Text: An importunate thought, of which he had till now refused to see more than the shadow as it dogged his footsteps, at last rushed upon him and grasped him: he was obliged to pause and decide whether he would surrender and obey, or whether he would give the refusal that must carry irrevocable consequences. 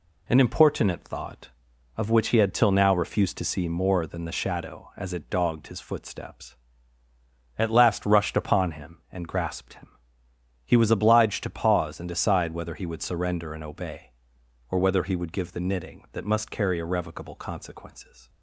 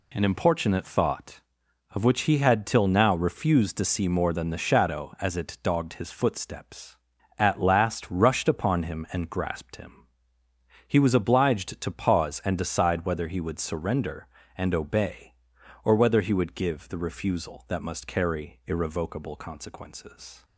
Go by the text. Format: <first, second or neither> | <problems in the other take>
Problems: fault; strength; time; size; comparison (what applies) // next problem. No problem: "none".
second | says "knitting" for "refusal"; at 15.5 s